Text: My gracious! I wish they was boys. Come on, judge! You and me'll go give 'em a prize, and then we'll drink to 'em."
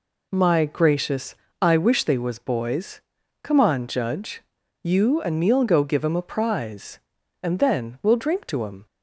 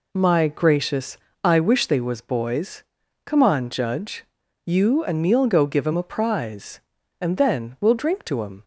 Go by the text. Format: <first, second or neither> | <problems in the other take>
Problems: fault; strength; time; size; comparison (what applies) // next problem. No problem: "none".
neither | none